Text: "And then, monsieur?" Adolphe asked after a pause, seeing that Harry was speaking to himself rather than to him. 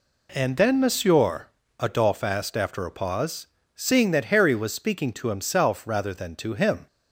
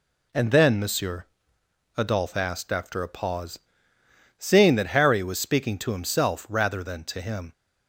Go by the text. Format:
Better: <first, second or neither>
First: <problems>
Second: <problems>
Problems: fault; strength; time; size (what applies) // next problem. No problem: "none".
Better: neither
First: none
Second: none